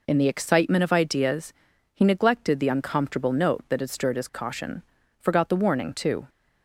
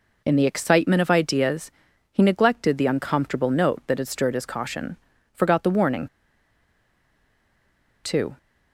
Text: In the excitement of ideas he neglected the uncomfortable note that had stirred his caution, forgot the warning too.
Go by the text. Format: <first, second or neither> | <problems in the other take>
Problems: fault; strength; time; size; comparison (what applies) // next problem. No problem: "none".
first | pauses between "ideas" and "he"; at 1.6 s; 0.44 s long; also in the first // pauses between "warning" and "too"; strong; at 6.0 s; 1.9 s long